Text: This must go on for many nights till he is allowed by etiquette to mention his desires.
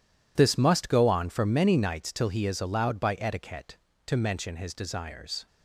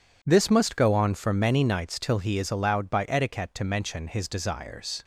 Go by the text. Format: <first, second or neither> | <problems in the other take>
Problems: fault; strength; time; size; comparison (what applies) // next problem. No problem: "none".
second | gets quieter; strong; throughout; 14 dB